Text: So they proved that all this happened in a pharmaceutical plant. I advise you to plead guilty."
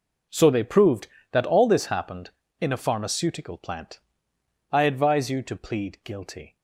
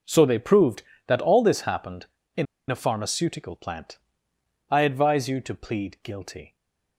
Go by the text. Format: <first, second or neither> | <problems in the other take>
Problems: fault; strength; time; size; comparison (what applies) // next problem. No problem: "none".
first | pauses between "in" and "a"; slight; at 2.4 s; 0.24 s long // stays silent after the last word; slight; from 6.4 s on; 0.5 s long